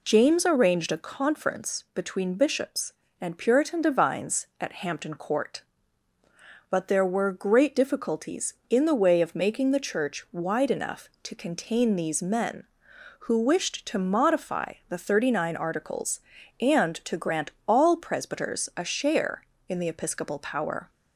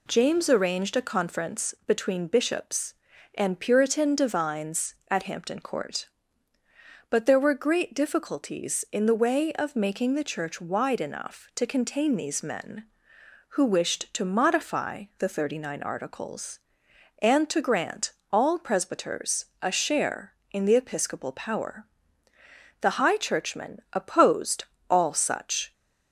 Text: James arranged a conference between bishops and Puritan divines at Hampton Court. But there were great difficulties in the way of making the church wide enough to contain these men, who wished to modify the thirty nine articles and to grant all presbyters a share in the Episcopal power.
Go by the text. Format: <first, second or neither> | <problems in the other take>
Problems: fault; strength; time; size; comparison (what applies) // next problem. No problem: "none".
first | pauses between "grant" and "all"; slight; at 18.1 s; 0.20 s long; slight in the first // pauses between "presbyters" and "a"; slight; at 19.4 s; 0.18 s long // goes on to say "The high churchmen opposed all such"; strong; from 22.8 s on; 2.9 s long